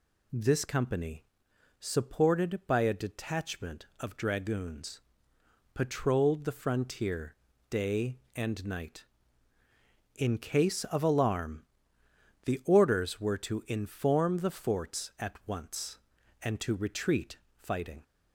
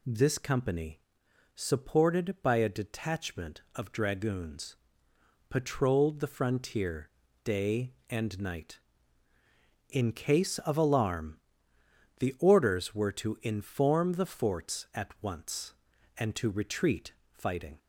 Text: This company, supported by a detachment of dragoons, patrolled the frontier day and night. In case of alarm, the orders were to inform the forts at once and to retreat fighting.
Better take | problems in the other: neither | pauses between "frontier" and "day"; slight; the same in both // pauses between "retreat" and "fighting"; slight; the same in both

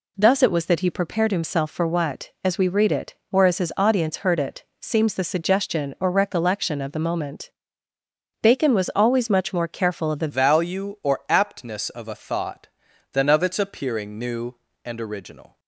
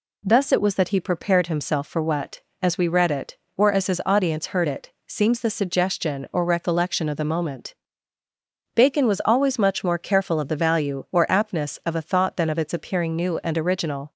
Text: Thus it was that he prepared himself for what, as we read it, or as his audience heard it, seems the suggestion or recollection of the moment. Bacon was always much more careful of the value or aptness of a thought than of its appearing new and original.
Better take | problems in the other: second | changes voice at "value"; from 10.2 s on; 5.3 s long

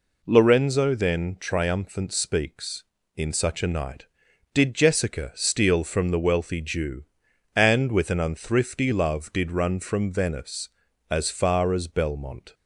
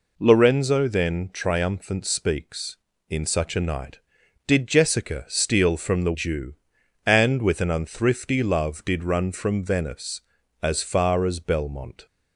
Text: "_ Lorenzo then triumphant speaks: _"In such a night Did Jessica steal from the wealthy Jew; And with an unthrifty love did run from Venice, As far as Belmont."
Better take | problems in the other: first | skips "wealthy"; at 6.1 s

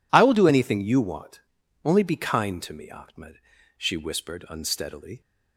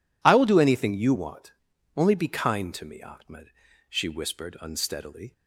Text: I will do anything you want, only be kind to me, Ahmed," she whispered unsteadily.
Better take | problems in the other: neither | none

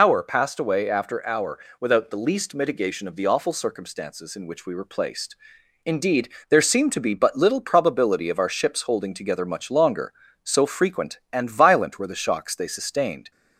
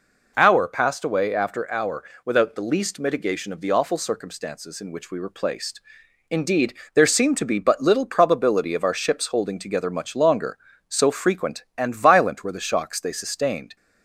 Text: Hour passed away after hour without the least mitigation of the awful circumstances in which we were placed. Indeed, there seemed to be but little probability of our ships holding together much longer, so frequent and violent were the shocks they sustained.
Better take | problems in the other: second | loses the start of "Hour"; at 0.0 s; 95 ms // pauses between "hour" and "without"; slight; at 1.5 s; 0.22 s long; slight in the second

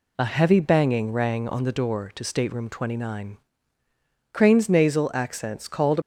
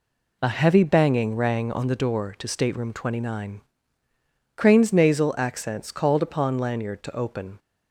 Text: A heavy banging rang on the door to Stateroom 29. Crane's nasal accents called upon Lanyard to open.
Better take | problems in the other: second | stops before "upon Lanyard to open"; at 6.0 s

